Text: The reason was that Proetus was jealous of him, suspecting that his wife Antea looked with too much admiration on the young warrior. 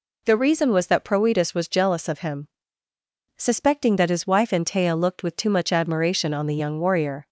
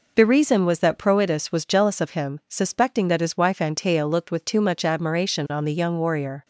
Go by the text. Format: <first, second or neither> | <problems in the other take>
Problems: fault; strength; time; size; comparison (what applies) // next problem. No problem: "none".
neither | none